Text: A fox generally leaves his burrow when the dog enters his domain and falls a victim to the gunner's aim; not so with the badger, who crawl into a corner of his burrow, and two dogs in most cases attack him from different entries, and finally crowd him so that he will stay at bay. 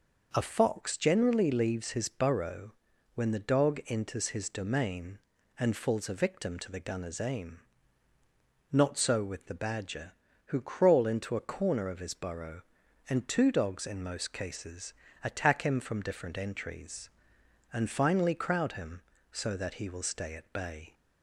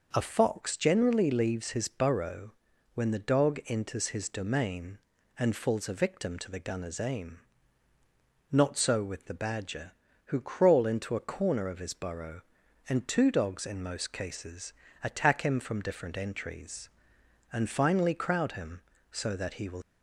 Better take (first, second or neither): first